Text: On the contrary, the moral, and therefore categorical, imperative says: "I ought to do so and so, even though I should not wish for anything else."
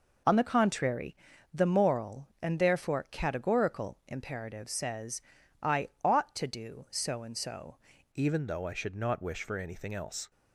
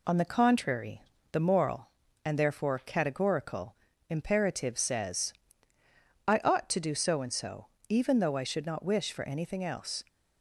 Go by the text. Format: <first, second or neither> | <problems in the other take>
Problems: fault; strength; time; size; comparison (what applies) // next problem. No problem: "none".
second | changes voice at "even"; from 8.1 s on; 2.2 s long